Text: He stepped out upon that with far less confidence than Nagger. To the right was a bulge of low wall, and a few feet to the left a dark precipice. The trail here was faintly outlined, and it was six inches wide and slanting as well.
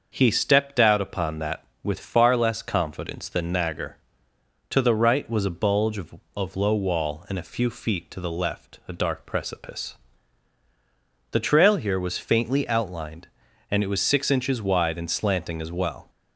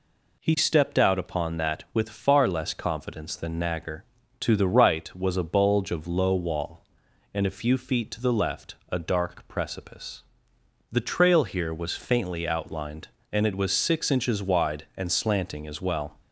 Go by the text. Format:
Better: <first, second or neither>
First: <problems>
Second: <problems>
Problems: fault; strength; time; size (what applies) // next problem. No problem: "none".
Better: second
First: starts louder than the rest; until 1.1 s; 6 dB // says "of" twice; at 6.3 s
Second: none